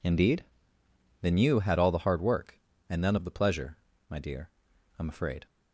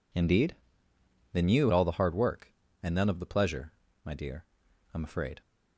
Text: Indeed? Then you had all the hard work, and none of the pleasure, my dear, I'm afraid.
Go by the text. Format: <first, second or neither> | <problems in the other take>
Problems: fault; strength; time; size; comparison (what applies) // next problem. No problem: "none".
first | skips "had"; at 1.7 s